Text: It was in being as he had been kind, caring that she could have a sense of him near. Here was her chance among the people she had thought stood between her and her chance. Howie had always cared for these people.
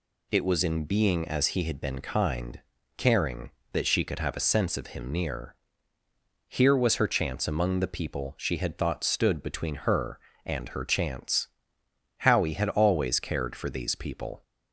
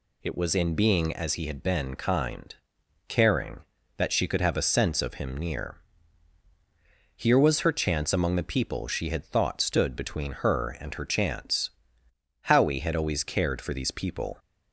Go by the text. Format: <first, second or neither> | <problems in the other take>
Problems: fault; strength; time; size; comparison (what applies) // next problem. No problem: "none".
neither | none